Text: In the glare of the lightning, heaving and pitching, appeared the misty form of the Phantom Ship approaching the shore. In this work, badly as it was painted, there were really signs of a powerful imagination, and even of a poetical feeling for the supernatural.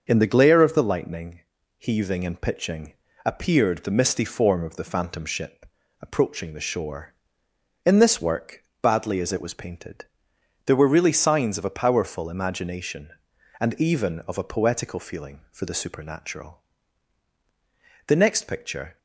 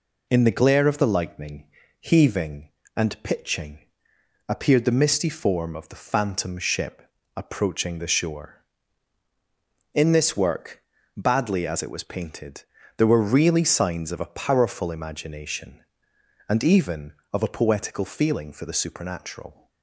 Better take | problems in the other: second | starts louder than the rest; until 1.0 s; 6.5 dB // pauses between "Ship" and "approaching"; slight; at 5.6 s; 0.34 s long; slight in the second // goes on to say "The next picture"; noticeable; from 18.0 s on; 0.92 s long

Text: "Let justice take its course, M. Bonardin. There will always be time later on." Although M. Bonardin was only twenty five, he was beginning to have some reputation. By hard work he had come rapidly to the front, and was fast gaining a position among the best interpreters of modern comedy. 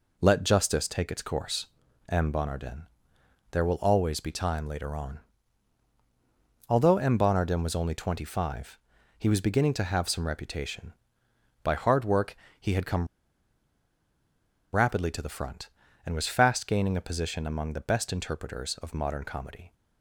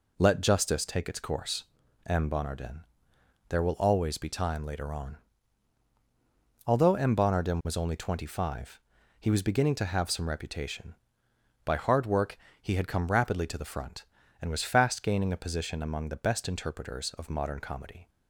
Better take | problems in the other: second | pauses between "work" and "he"; slight; at 12.3 s; 0.24 s long; slight in the second // pauses between "come" and "rapidly"; strong; at 13.0 s; 1.6 s long

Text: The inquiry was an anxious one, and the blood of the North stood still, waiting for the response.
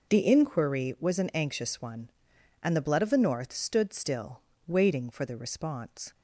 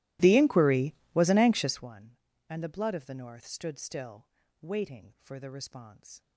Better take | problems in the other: first | starts louder than the rest; strong; until 1.9 s; 17 dB

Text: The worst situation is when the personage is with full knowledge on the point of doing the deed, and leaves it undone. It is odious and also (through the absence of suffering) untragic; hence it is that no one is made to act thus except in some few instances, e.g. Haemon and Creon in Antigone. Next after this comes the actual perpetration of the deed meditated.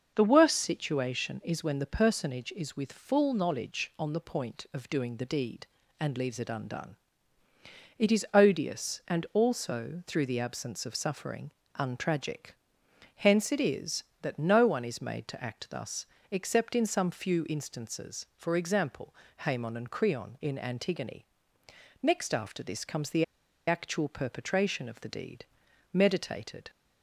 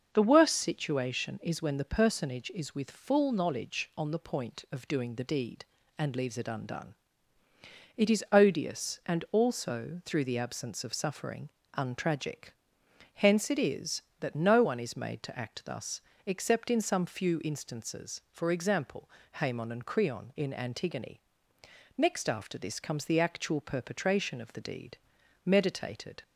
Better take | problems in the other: second | starts louder than the rest; until 1.1 s; 6.5 dB; also in the second // pauses between "thus" and "except"; slight; at 16.0 s; 0.24 s long; slight in the second // pauses between "the" and "actual"; at 23.2 s; 0.43 s long // pauses between "deed" and "meditated"; noticeable; at 25.4 s; 0.48 s long; noticeable in the second

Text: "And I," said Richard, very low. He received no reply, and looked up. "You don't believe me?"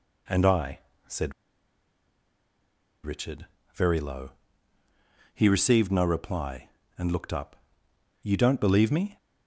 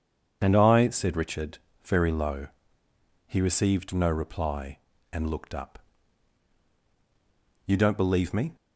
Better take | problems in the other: second | pauses between "said" and "Richard"; strong; at 1.3 s; 1.7 s long

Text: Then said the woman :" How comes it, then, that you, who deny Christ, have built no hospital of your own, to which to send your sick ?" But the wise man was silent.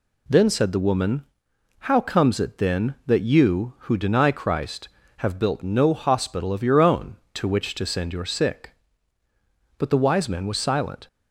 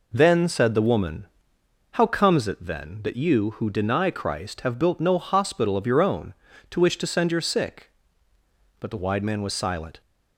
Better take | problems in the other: first | says "wide" for "wise"; at 9.0 s

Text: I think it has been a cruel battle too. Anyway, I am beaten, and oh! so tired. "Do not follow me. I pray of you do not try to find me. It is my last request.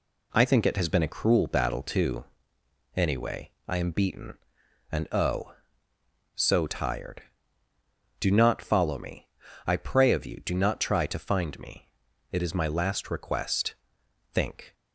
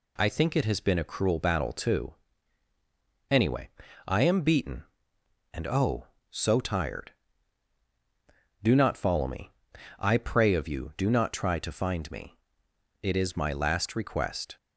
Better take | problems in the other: second | goes on to say "Think"; slight; from 14.3 s on; 0.42 s long

